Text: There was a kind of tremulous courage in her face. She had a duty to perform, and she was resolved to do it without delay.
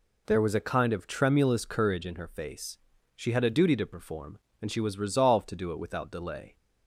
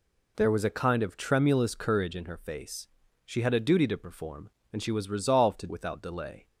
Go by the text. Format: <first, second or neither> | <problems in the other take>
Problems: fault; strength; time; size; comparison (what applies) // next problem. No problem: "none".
first | skips "do it"; at 5.6 s